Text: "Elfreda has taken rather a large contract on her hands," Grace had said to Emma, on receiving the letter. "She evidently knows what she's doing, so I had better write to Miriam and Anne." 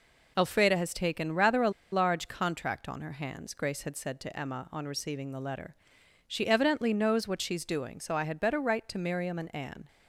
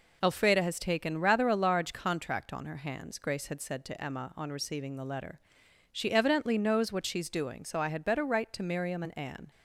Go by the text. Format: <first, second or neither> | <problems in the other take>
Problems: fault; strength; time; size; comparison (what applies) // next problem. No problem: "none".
second | pauses between "a" and "large"; slight; at 1.6 s; 0.22 s long